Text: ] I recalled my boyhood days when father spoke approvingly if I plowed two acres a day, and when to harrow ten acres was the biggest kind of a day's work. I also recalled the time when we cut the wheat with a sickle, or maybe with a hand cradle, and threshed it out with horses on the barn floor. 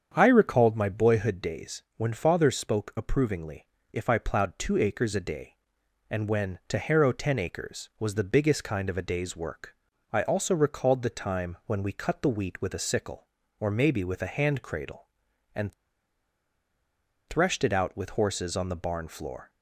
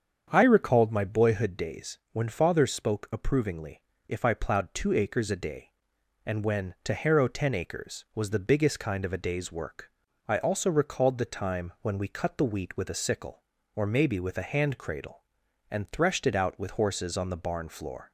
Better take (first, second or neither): second